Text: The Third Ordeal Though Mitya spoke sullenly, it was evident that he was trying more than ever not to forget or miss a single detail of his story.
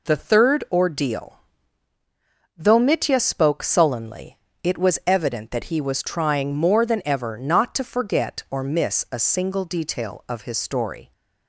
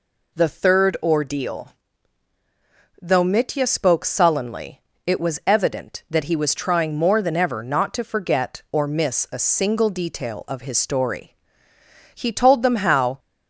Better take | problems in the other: first | pauses between "Ordeal" and "Though"; strong; at 1.7 s; 1.3 s long; also in the first // goes on to say "He told them how"; noticeable; from 12.1 s on; 1.0 s long

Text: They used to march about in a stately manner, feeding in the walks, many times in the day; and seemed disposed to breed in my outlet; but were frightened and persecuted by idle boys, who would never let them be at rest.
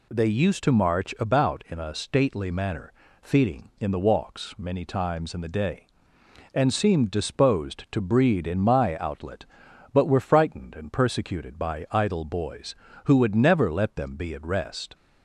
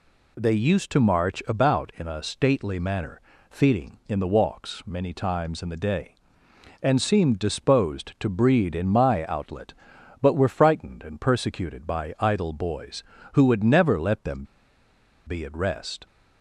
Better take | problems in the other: first | pauses between "them" and "be"; noticeable; at 14.4 s; 0.82 s long

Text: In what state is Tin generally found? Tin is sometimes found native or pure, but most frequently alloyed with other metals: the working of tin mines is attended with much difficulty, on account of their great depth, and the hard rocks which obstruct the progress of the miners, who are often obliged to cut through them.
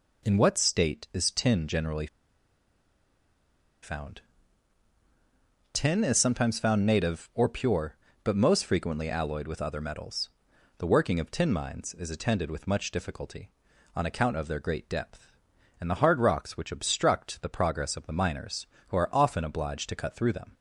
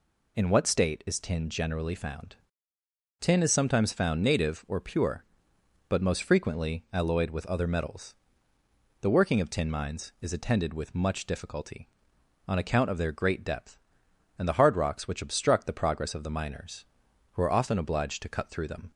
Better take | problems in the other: second | pauses between "generally" and "found"; strong; at 2.0 s; 1.7 s long

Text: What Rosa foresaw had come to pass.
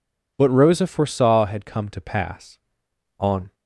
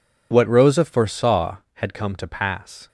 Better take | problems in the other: second | goes on to say "On"; slight; from 3.1 s on; 0.34 s long

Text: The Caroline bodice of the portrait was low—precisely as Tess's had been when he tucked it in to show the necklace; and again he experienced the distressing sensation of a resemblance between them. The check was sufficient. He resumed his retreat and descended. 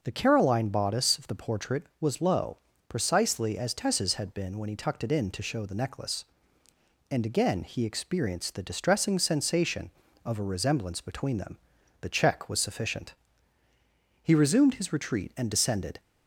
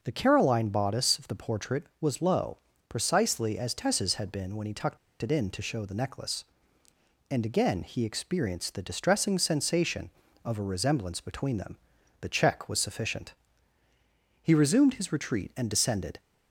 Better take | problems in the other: first | pauses between "tucked" and "it"; slight; at 4.9 s; 0.23 s long

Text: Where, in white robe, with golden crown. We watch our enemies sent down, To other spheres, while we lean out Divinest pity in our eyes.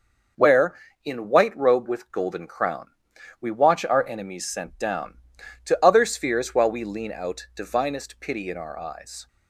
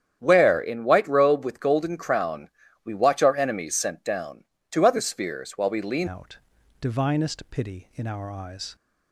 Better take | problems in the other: first | starts louder than the rest; strong; until 1.2 s; 9 dB // changes voice at "out"; from 6.0 s on; 2.7 s long // pauses between "out" and "Divinest"; at 6.3 s; 0.44 s long

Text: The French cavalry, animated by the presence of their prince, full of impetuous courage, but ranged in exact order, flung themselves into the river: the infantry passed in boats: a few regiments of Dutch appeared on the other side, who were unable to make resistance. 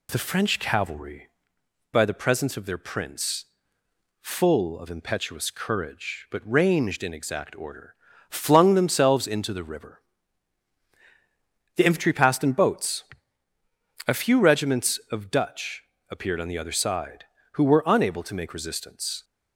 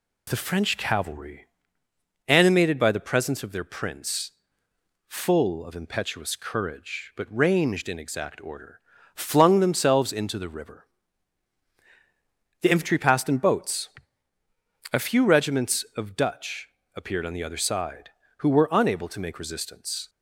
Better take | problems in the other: second | skips "animated"; at 1.6 s // pauses between "Dutch" and "appeared"; slight; at 15.8 s; 0.22 s long; slight in the second

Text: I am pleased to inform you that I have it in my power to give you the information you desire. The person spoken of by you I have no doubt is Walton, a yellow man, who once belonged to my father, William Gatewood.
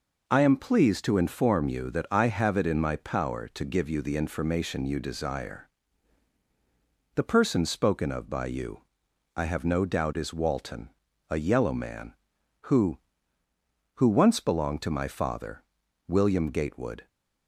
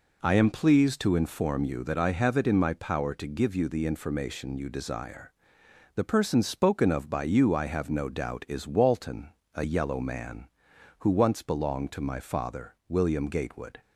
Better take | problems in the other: second | pauses between "you" and "I"; noticeable; at 8.8 s; 0.56 s long // says "who" twice; at 13.9 s

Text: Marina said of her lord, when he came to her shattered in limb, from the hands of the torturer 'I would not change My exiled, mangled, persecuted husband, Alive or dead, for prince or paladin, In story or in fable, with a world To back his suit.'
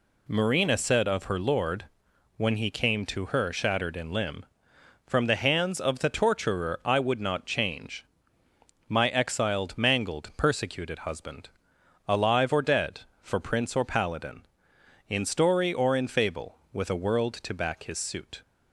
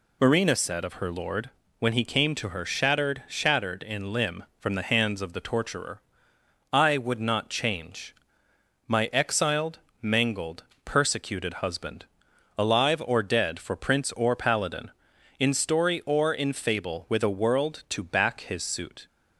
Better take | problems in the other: first | says "shattered" twice; at 3.2 s // pauses between "torturer" and "I"; noticeable; at 6.0 s; 0.72 s long // pauses between "change" and "My"; noticeable; at 8.1 s; 0.76 s long; noticeable in the first

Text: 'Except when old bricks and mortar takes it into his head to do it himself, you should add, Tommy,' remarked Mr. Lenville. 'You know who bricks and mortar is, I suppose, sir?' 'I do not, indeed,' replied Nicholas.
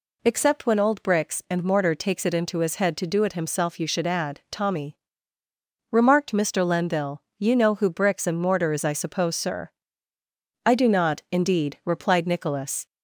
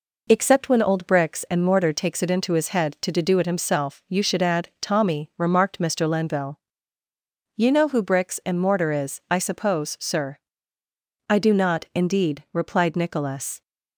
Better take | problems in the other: first | says "to" twice; at 3.1 s

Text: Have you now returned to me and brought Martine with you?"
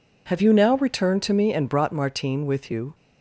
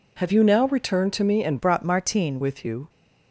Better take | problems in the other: first | changes voice from "brought" to "Martine"; from 1.5 to 2.3 s; 0.8 s long

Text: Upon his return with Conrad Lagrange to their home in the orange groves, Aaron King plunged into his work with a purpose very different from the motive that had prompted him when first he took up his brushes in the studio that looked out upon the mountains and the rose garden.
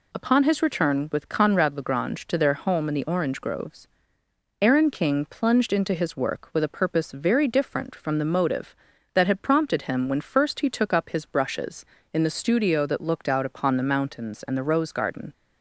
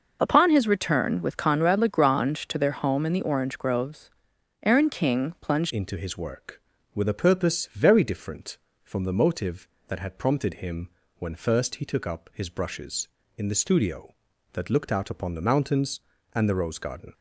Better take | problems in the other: first | changes voice at "into"; from 5.6 s on; 11.5 s long // pauses between "him" and "when"; slight; at 10.8 s; 0.30 s long

